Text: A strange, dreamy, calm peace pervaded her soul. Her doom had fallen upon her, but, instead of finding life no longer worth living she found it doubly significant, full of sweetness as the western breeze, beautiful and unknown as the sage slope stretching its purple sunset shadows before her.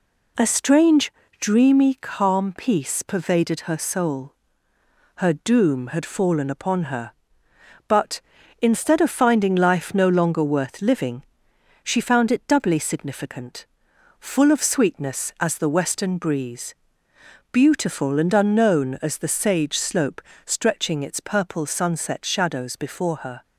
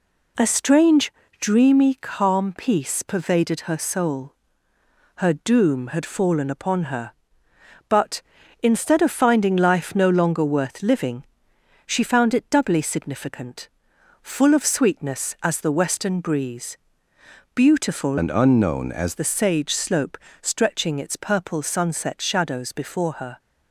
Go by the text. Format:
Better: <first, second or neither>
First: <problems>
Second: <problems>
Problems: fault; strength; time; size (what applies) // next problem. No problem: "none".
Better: first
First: pauses between "living" and "she"; noticeable; at 11.2 s; 0.62 s long // pauses between "slope" and "stretching"; slight; at 20.2 s; 0.24 s long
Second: pauses between "living" and "she"; noticeable; at 11.2 s; 0.64 s long // changes voice from "and" to "as"; from 18.1 to 19.1 s; 1.0 s long // pauses between "slope" and "stretching"; slight; at 20.1 s; 0.24 s long